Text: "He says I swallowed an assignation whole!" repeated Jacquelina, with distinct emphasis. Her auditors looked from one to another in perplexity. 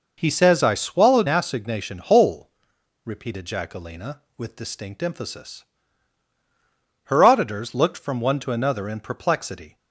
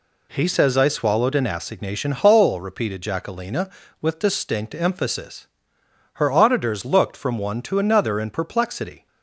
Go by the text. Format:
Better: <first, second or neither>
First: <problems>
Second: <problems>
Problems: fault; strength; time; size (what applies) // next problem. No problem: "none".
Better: second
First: skips "an"; at 1.2 s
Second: none